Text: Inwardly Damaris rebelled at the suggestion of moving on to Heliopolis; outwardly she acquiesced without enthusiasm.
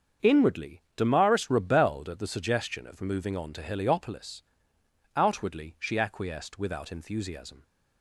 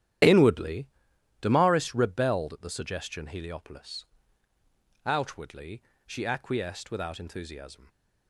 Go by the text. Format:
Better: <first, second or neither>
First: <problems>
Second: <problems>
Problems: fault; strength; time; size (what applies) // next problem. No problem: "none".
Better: first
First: starts louder than the rest; strong; until 1.3 s; 7 dB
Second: starts louder than the rest; strong; until 1.7 s; 11 dB // pauses between "Inwardly" and "Damaris"; noticeable; at 0.8 s; 0.54 s long // skips "of moving on to"; at 3.2 s // pauses between "outwardly" and "she"; slight; at 5.8 s; 0.24 s long